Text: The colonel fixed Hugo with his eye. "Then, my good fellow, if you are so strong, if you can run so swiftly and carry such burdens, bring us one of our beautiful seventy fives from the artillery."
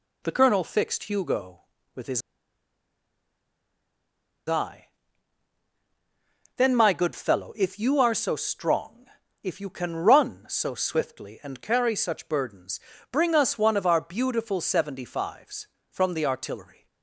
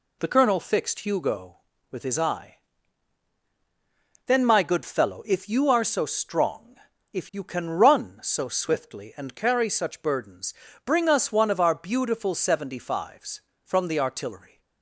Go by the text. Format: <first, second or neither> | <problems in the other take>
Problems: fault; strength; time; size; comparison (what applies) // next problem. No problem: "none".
second | pauses between "his" and "eye"; strong; at 2.2 s; 2.2 s long